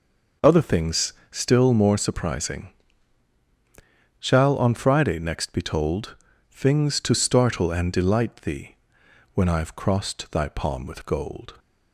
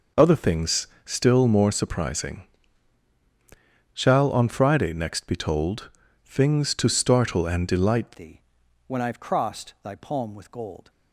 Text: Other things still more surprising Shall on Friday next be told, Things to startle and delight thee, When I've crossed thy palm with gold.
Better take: first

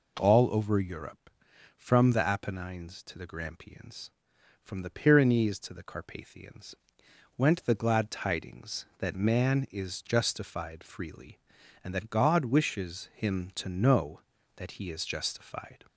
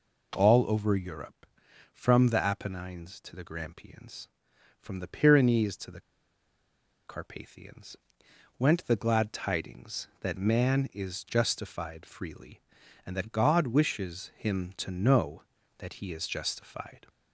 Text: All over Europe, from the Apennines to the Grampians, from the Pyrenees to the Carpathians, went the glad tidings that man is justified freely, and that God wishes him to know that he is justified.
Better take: first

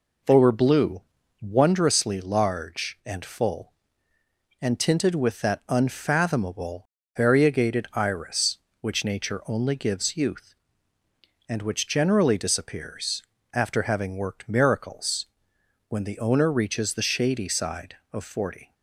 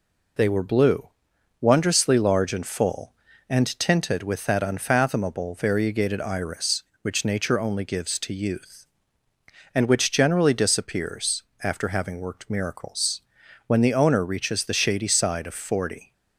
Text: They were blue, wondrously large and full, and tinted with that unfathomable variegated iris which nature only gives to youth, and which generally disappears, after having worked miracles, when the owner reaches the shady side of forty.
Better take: second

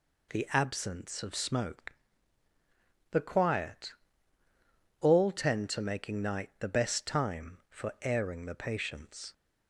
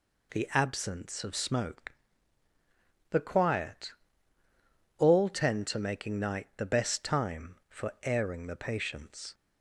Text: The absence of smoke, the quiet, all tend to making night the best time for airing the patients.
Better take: neither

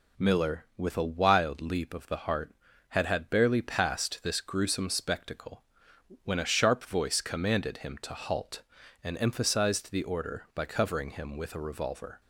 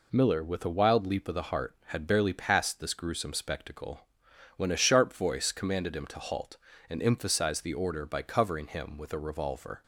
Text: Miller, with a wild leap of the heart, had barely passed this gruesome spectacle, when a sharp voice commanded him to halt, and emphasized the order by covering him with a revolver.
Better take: second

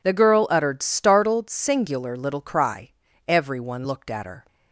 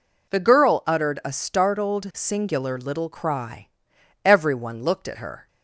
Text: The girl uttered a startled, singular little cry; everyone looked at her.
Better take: second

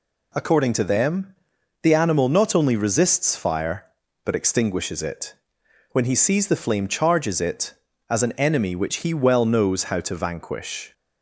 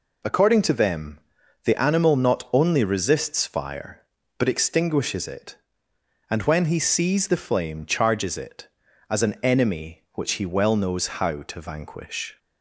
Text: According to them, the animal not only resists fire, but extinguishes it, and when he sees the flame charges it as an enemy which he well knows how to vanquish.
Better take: second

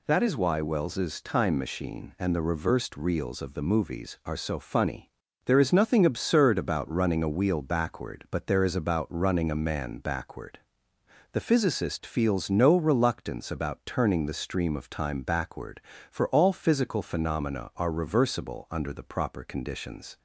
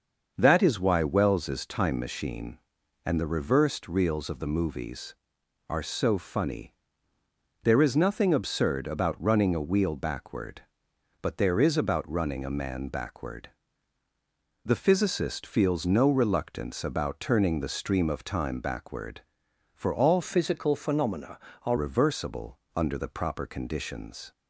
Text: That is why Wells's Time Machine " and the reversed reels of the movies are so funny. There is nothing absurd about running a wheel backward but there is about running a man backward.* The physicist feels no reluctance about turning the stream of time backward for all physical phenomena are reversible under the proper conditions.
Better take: first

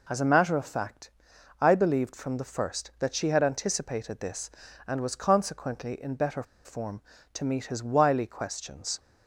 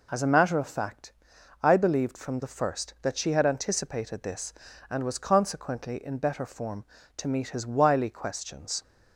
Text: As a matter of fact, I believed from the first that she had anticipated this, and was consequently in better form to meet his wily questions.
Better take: second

